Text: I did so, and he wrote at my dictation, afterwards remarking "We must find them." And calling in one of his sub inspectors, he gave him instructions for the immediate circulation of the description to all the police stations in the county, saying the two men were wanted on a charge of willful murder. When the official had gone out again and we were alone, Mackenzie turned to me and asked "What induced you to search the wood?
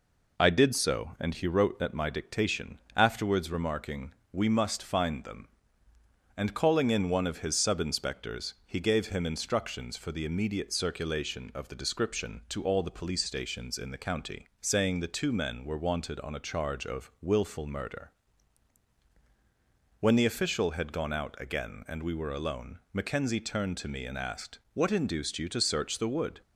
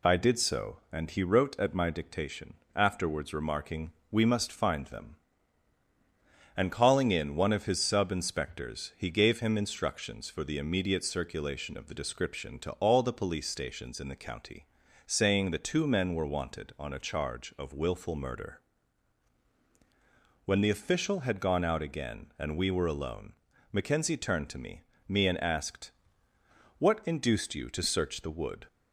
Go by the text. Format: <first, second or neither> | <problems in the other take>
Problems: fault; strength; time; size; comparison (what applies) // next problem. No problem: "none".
first | pauses between "remarking" and "We"; slight; at 3.9 s; 0.18 s long; slight in the first // says "me" twice; at 25.0 s // pauses between "asked" and "What"; noticeable; at 25.9 s; 0.86 s long; slight in the first